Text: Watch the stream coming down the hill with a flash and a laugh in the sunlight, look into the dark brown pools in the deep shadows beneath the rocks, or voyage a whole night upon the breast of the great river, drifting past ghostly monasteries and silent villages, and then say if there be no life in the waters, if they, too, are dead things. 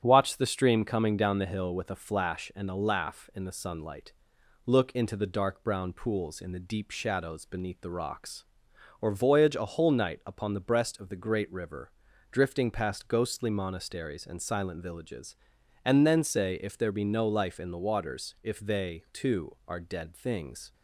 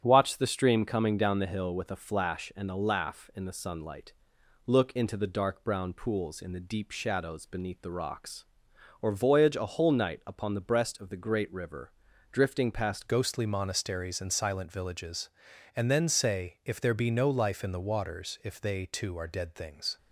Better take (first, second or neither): first